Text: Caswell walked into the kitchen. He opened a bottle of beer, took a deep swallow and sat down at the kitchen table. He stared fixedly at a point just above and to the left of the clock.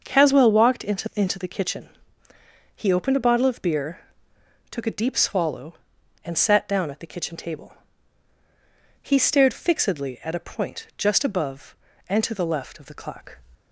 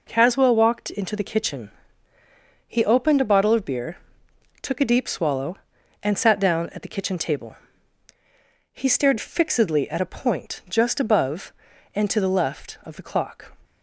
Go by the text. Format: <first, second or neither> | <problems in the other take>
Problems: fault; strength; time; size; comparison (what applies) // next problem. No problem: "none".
second | starts louder than the rest; until 1.0 s; 6.5 dB // says "into" twice; at 1.1 s